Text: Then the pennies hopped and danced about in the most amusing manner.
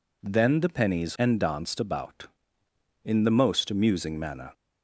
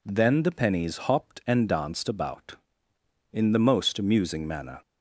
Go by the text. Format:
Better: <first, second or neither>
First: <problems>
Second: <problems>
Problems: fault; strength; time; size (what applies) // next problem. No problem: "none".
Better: second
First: skips "hopped"; at 1.1 s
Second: none